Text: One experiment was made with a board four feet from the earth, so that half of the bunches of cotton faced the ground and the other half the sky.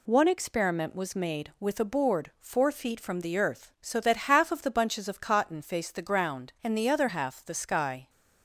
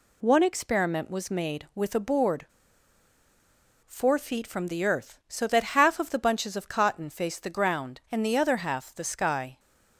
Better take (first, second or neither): first